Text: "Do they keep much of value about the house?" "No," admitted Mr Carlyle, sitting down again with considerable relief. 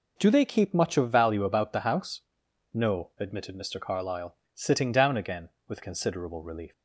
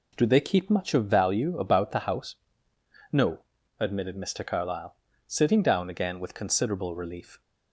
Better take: neither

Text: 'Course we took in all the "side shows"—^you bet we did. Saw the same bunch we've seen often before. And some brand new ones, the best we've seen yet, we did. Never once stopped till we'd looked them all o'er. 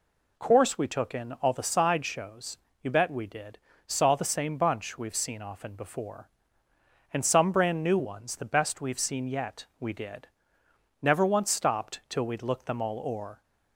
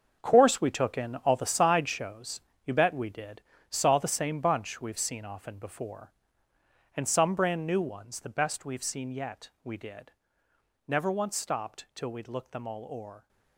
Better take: first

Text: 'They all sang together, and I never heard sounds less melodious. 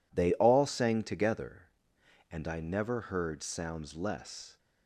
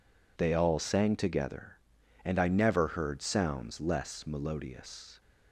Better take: second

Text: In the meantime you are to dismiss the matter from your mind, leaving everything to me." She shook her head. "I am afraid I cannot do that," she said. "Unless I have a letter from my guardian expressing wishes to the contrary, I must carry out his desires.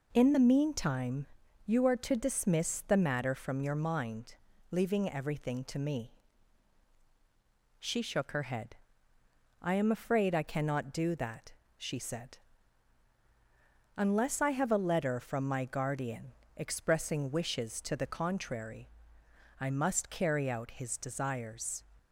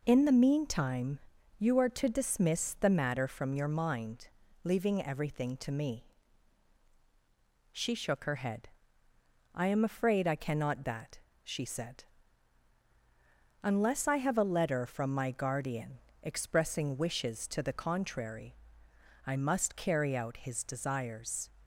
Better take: first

